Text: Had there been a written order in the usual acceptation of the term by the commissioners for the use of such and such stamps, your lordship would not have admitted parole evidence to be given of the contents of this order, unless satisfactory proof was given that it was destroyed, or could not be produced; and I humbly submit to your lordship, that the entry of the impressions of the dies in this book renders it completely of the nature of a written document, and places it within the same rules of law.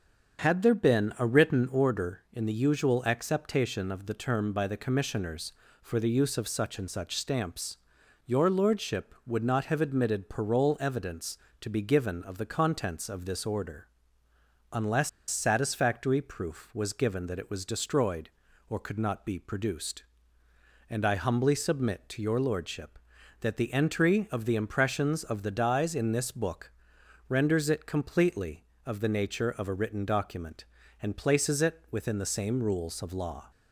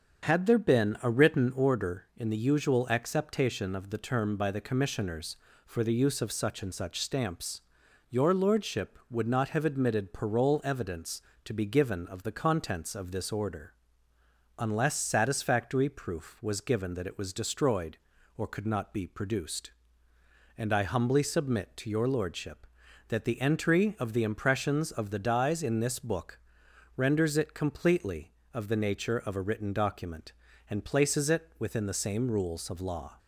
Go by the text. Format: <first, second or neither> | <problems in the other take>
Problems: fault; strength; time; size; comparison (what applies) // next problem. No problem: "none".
second | starts louder than the rest; strong; until 1.4 s; 7.5 dB; strong in the second // pauses between "unless" and "satisfactory"; slight; at 15.0 s; 0.20 s long // pauses between "book" and "renders"; noticeable; at 26.7 s; 0.56 s long; noticeable in the second